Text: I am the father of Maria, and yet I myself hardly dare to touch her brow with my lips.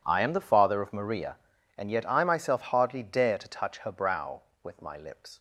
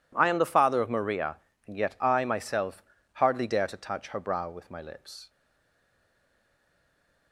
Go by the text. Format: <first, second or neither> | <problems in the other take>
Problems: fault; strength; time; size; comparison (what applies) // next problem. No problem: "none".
first | pauses between "myself" and "hardly"; slight; at 2.8 s; 0.30 s long // stays silent after the last word; noticeable; from 5.2 s on; 2.1 s long